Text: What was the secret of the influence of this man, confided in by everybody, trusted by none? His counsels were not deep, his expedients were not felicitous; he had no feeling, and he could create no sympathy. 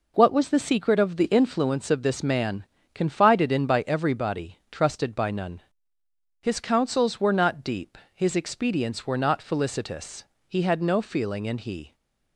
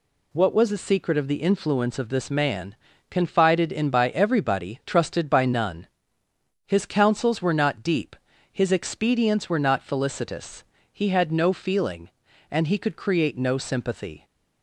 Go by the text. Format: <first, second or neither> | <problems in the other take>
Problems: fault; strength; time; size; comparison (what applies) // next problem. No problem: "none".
second | stops before "could create no sympathy"; at 11.9 s